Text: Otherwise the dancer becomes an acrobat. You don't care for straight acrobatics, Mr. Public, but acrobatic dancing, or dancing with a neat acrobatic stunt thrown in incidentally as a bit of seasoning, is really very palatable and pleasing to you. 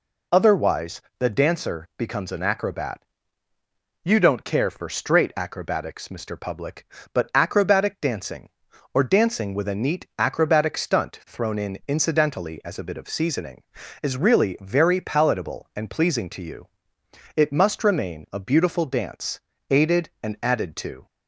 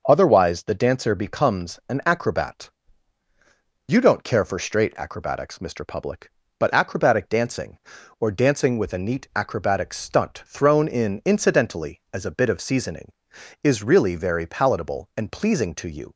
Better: second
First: pauses between "Otherwise" and "the"; slight; at 1.0 s; 0.18 s long // goes on to say "It must remain a beautiful dance aided and added to"; strong; from 17.3 s on; 3.7 s long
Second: none

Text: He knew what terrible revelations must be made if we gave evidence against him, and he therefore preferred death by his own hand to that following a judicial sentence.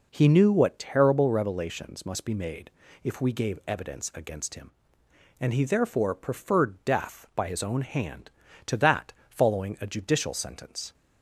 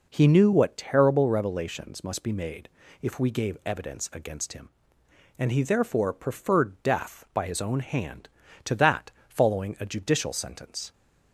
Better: neither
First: pauses between "made" and "if"; slight; at 2.7 s; 0.34 s long // pauses between "that" and "following"; slight; at 9.1 s; 0.17 s long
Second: pauses between "made" and "if"; slight; at 2.6 s; 0.34 s long // pauses between "that" and "following"; slight; at 9.1 s; 0.18 s long

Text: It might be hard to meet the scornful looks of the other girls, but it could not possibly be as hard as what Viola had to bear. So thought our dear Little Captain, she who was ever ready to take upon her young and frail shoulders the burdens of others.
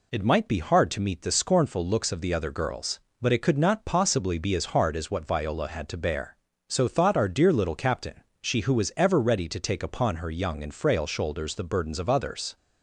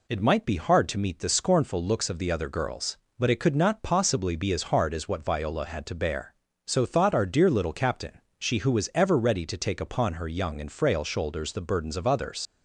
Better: first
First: none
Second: leaves "others" unfinished; at 12.4 s; 80 ms

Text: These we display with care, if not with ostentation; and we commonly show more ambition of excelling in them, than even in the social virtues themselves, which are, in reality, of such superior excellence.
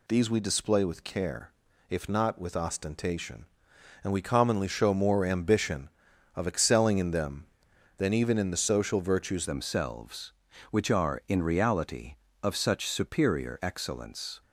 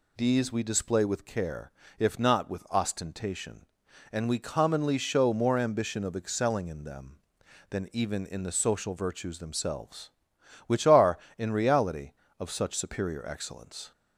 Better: second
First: changes voice at "themselves"; from 9.4 s on; 5.0 s long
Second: none

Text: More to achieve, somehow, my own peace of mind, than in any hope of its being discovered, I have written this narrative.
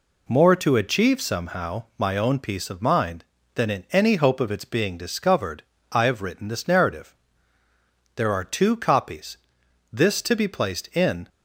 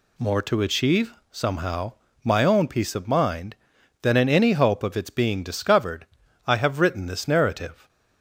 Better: second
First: goes on to say "There are two copies this to be placed in"; strong; from 8.1 s on; 3.1 s long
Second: none

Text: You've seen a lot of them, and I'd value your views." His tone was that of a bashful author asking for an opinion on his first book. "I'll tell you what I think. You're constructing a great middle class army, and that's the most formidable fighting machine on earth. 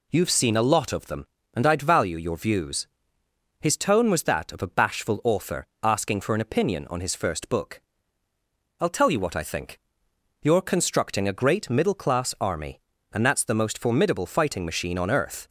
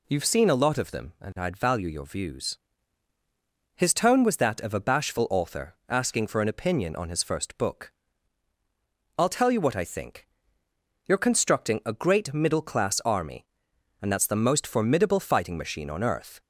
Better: neither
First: pauses between "author" and "asking"; slight; at 5.6 s; 0.16 s long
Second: pauses between "author" and "asking"; slight; at 5.7 s; 0.16 s long

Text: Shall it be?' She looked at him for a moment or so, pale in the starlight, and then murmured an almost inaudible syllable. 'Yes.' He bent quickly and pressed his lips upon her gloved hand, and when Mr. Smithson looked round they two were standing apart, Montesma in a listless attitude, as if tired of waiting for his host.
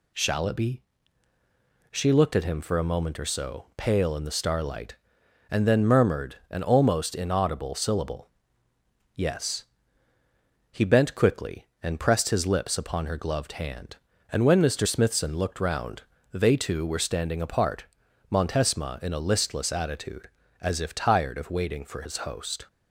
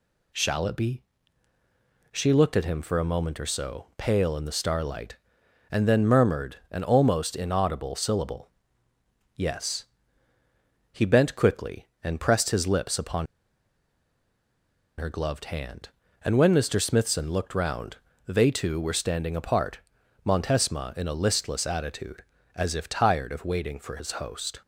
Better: first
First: pauses between "round" and "they"; slight; at 16.0 s; 0.30 s long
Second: pauses between "upon" and "her"; strong; at 13.2 s; 1.7 s long // pauses between "round" and "they"; slight; at 17.9 s; 0.30 s long

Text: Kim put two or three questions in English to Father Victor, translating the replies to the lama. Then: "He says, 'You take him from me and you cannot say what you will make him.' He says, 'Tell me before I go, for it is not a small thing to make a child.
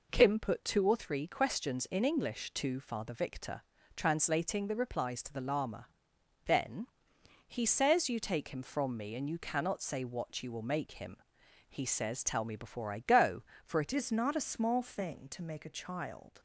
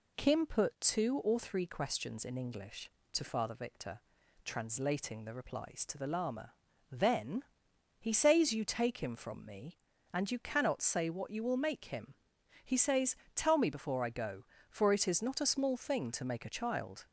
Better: second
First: changes voice at "is"; from 13.9 s on; 2.4 s long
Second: none

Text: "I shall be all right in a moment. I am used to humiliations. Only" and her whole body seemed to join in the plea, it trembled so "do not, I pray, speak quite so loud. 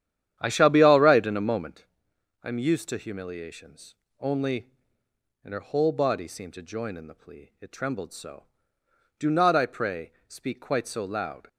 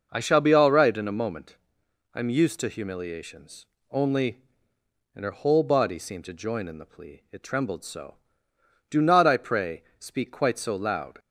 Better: second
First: starts louder than the rest; strong; until 1.8 s; 10 dB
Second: none

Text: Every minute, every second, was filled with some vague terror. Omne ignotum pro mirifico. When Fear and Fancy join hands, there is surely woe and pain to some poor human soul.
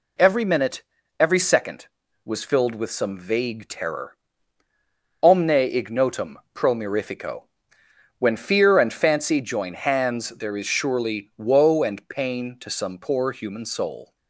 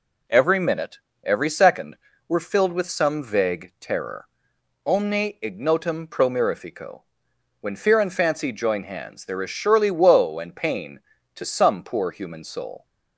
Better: first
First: none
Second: says "were" for "was"; at 2.2 s

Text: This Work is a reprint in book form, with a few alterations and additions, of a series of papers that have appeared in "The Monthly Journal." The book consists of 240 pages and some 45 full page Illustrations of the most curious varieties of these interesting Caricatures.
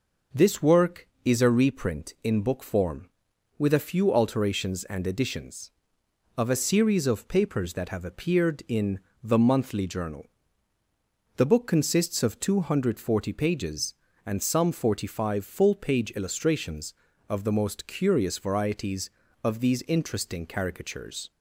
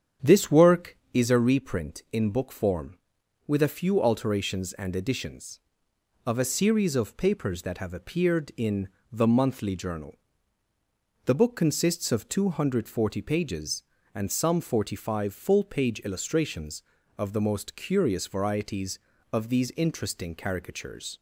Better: first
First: pauses between "in" and "The"; slight; at 8.9 s; 0.24 s long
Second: starts louder than the rest; strong; until 1.2 s; 8.5 dB // pauses between "in" and "The"; slight; at 8.8 s; 0.24 s long

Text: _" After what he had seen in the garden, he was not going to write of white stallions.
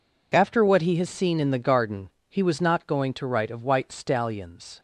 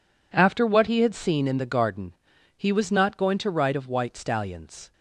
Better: second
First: says "has" for "had"; at 0.9 s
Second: none

